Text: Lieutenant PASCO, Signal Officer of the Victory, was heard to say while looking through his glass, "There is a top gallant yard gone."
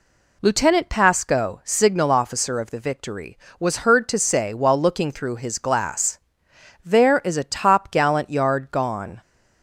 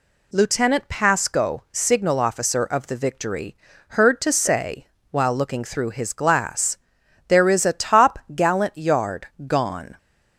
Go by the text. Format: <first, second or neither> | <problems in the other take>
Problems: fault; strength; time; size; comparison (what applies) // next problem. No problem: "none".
first | skips "was"; at 3.7 s // pauses between "say" and "while"; slight; at 4.8 s; 0.24 s long // pauses between "top" and "gallant"; slight; at 8.1 s; 0.16 s long // pauses between "yard" and "gone"; slight; at 9.2 s; 0.18 s long